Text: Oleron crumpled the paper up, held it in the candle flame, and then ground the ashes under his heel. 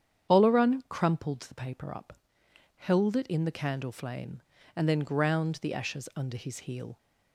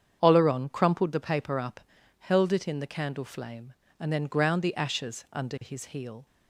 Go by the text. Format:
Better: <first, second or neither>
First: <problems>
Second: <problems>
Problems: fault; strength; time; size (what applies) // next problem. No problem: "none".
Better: neither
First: starts louder than the rest; strong; until 1.3 s; 8.5 dB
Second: starts louder than the rest; strong; until 1.2 s; 8 dB